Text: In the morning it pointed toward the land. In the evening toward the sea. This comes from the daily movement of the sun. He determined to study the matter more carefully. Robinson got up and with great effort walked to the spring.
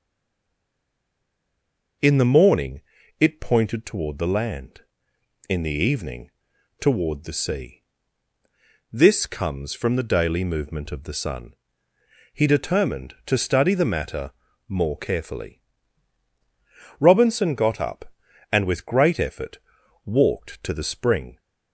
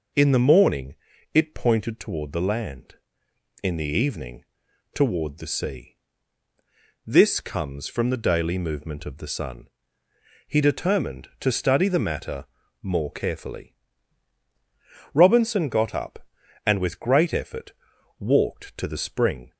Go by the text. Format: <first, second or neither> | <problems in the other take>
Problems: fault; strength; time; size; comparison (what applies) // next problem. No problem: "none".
second | stays silent before the first word; noticeable; until 2.0 s; 2.0 s long // pauses between "morning" and "it"; at 2.8 s; 0.38 s long; also in the second // pauses between "evening" and "toward"; noticeable; at 6.2 s; 0.50 s long; noticeable in the second // pauses between "matter" and "more"; at 14.3 s; 0.38 s long; also in the second // pauses between "effort" and "walked"; noticeable; at 19.5 s; 0.46 s long; noticeable in the second